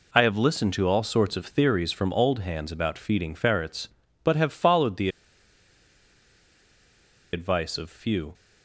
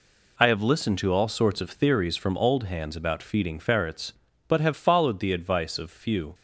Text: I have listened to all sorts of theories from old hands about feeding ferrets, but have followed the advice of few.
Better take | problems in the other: second | pauses between "the" and "advice"; strong; at 5.0 s; 2.2 s long

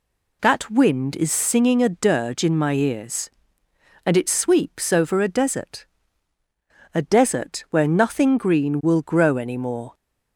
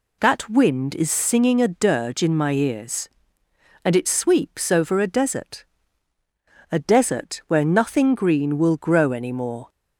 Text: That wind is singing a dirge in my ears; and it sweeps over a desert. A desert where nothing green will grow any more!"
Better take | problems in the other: neither | none

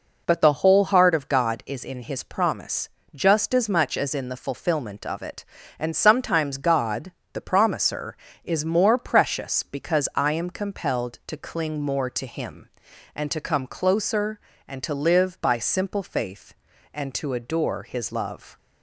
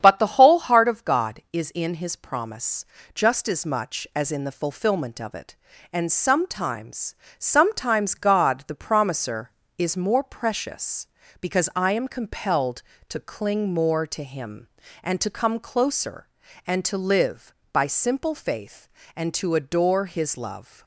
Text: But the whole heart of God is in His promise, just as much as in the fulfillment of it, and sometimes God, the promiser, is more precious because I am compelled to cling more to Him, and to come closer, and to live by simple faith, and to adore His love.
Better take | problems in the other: first | starts louder than the rest; strong; until 1.0 s; 8.5 dB // says "sometimes" twice; at 7.3 s

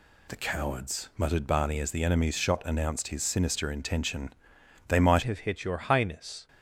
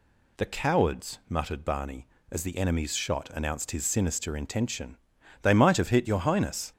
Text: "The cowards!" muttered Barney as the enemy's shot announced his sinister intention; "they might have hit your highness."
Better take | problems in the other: second | changes voice at "have"; from 5.2 s on; 1.2 s long

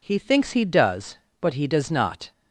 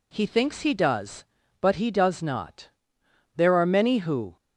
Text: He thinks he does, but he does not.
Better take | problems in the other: first | goes on to say "There are many who"; noticeable; from 3.3 s on; 1.0 s long

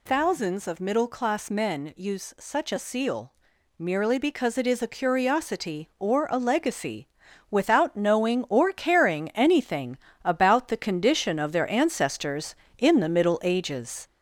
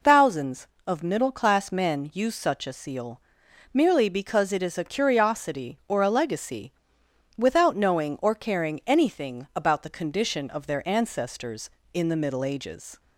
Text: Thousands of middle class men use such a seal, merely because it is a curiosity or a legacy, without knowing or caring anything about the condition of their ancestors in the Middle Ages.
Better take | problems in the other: second | gets louder; throughout; 3.5 dB // pauses between "anything" and "about"; slight; at 9.9 s; 0.26 s long

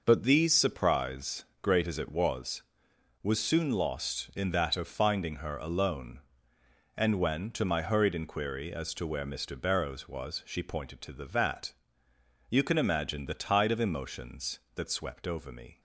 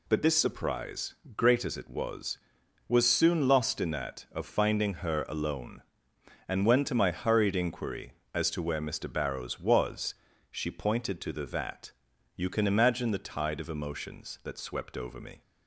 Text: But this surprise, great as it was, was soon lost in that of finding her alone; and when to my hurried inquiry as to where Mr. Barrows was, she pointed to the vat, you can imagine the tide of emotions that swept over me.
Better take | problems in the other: second | says "these" for "this"; at 0.2 s

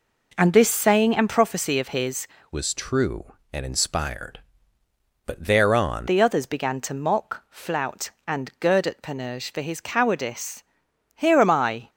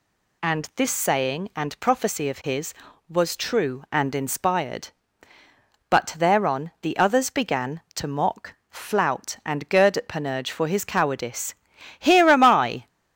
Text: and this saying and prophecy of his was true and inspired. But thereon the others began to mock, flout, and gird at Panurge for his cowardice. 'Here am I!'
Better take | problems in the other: second | changes voice from "was" to "thereon"; from 2.5 to 6.0 s; 3.5 s long

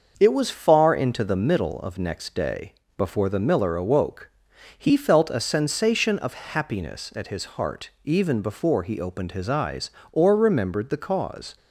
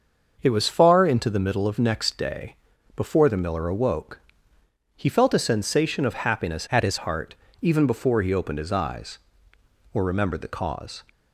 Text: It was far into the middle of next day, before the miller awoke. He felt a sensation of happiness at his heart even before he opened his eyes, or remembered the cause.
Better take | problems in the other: first | starts louder than the rest; until 1.4 s; 6.5 dB; noticeable in the first // changes voice from "at" to "his"; from 6.6 to 6.9 s; 0.3 s long // pauses between "heart" and "even"; slight; at 7.3 s; 0.26 s long

